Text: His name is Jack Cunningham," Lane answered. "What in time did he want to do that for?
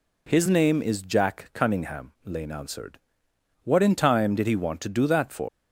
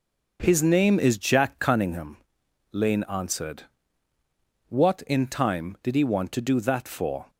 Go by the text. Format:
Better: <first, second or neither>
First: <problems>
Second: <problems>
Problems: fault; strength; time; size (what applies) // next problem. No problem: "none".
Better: second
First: leaves "for" unfinished; at 5.4 s; 125 ms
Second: none